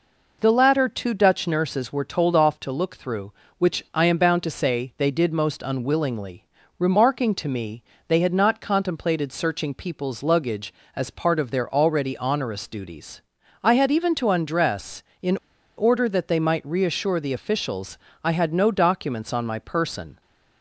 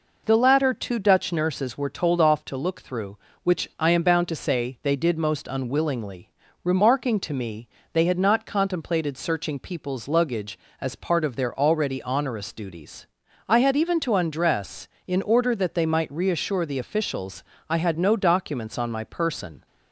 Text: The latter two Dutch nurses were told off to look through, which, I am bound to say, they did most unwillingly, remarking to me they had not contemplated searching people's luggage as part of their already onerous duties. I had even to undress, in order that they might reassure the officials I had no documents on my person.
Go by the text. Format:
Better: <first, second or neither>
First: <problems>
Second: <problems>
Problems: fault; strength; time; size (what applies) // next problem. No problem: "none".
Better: second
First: pauses between "me" and "they"; slight; at 7.8 s; 0.24 s long // pauses between "in" and "order"; at 15.3 s; 0.41 s long // pauses between "officials" and "I"; slight; at 17.9 s; 0.24 s long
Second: pauses between "me" and "they"; slight; at 7.6 s; 0.24 s long // pauses between "officials" and "I"; slight; at 17.4 s; 0.24 s long